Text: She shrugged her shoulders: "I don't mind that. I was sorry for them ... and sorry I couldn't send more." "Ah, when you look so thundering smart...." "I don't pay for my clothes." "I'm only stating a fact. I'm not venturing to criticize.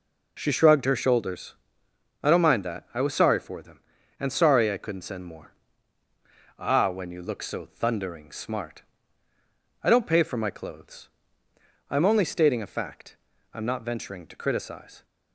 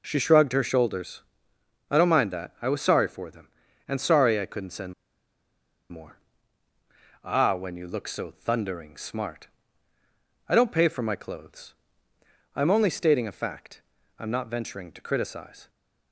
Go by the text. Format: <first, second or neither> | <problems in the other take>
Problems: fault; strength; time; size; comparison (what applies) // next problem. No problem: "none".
first | pauses between "send" and "more"; noticeable; at 4.9 s; 0.96 s long